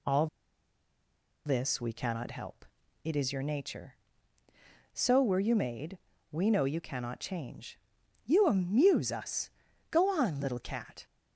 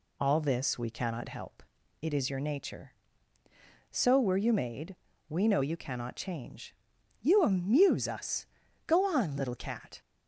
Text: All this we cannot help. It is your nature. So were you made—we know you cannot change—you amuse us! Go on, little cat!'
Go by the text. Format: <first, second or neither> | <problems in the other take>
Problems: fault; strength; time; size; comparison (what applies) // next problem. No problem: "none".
second | pauses between "All" and "this"; at 0.2 s; 1.1 s long